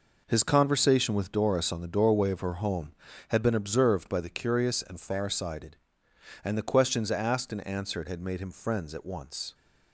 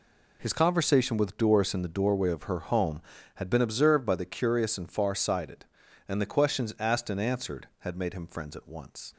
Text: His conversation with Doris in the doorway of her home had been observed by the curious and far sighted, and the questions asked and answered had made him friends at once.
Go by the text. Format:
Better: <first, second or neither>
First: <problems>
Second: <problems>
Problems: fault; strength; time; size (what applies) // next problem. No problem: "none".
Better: second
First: says "on" for "in"; at 1.7 s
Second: none